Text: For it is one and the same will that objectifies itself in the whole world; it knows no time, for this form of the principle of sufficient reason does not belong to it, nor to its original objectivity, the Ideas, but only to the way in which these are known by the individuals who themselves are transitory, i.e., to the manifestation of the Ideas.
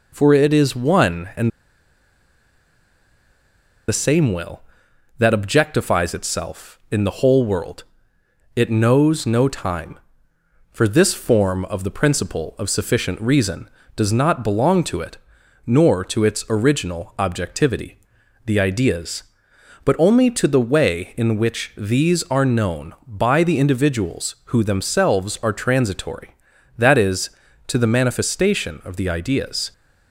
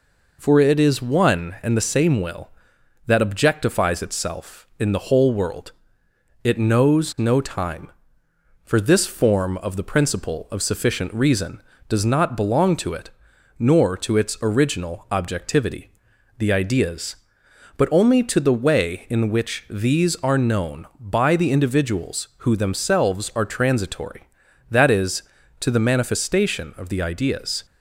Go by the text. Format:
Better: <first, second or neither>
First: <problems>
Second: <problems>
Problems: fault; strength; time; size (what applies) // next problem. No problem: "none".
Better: second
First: pauses between "and" and "the"; strong; at 1.4 s; 2.3 s long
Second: none